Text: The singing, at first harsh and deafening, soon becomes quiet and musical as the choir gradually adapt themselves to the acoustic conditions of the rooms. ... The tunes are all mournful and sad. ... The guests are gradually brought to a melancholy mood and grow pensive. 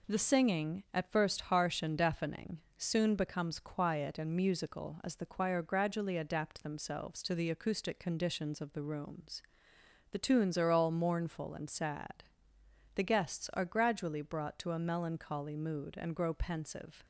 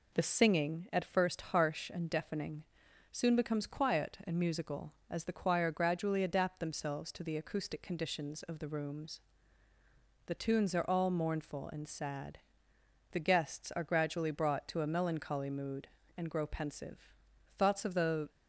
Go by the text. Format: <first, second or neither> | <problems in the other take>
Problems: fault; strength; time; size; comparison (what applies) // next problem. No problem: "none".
first | goes on to say "Thoughts of the"; noticeable; from 17.5 s on; 0.72 s long